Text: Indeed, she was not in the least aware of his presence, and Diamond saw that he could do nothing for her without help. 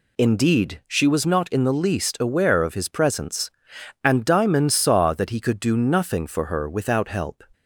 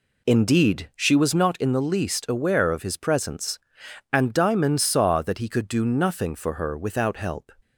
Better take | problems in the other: first | starts louder than the rest; slight; until 1.7 s; 2.5 dB

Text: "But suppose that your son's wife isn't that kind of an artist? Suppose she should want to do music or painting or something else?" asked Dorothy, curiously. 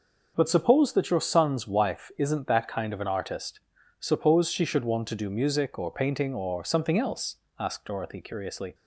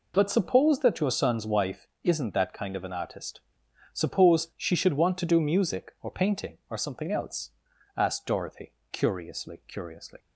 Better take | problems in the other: first | pauses between "wife" and "isn't"; slight; at 1.8 s; 0.18 s long // says "curiously" twice; at 9.6 s

